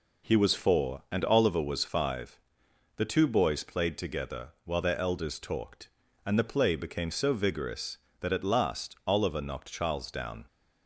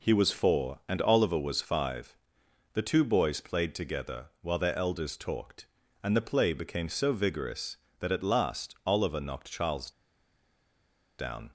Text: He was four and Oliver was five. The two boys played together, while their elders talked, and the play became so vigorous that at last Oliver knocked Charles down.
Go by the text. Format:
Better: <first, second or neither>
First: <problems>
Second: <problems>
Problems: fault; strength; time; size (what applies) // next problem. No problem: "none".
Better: first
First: none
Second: pauses between "Charles" and "down"; strong; at 9.9 s; 1.2 s long